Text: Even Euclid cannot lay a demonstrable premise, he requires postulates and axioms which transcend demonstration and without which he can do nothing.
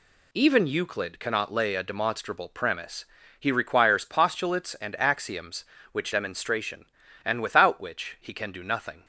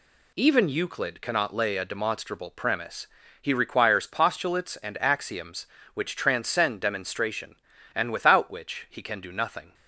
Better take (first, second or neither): second